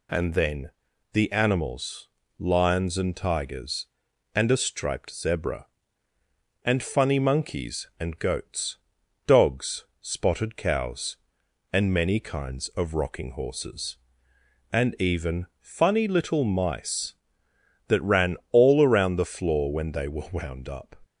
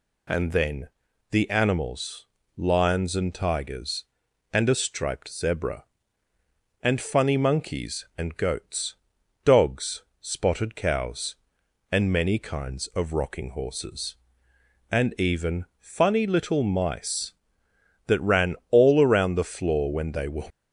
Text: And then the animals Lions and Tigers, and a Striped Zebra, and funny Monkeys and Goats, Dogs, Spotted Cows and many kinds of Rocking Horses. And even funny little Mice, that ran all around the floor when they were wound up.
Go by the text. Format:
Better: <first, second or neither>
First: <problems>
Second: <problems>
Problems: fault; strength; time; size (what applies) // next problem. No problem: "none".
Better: first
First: pauses between "then" and "the"; at 0.7 s; 0.42 s long // pauses between "animals" and "Lions"; slight; at 2.0 s; 0.34 s long // pauses between "ran" and "all"; slight; at 18.3 s; 0.16 s long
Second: pauses between "then" and "the"; at 0.8 s; 0.42 s long // pauses between "animals" and "Lions"; slight; at 2.2 s; 0.34 s long // pauses between "ran" and "all"; slight; at 18.5 s; 0.16 s long // stops before "wound up"; at 20.5 s